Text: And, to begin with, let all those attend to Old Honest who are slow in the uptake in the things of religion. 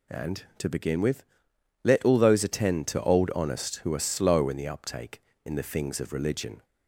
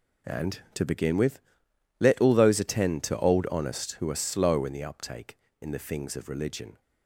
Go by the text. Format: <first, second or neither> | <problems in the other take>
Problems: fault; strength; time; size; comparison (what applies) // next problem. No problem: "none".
first | gets quieter; strong; throughout; 13 dB